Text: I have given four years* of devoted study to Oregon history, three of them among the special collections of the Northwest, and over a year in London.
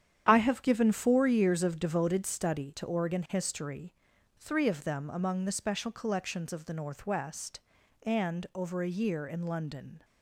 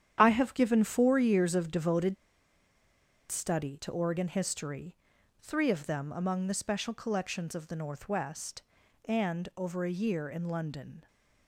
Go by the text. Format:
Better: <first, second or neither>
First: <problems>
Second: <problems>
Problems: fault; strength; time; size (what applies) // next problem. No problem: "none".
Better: first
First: starts louder than the rest; strong; until 1.3 s; 8.5 dB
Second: starts louder than the rest; strong; until 1.2 s; 9 dB // pauses between "devoted" and "study"; at 2.1 s; 1.1 s long